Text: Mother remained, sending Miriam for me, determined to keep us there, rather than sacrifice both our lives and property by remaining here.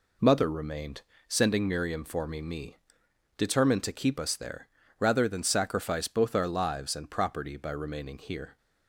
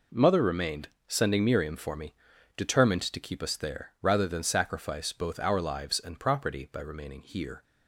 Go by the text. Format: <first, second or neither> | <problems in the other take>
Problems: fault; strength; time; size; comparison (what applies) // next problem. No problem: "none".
second | says "me" twice; at 2.4 s